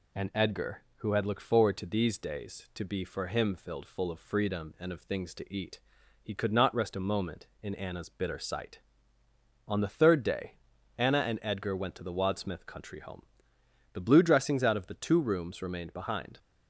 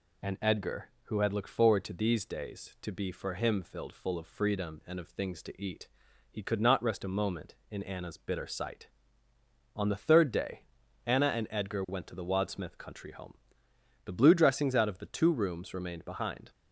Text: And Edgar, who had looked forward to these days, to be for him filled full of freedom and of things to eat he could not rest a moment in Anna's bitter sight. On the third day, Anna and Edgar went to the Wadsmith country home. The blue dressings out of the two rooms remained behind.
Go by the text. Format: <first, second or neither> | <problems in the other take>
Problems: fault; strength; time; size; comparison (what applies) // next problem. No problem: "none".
neither | pauses between "eat" and "he"; the same in both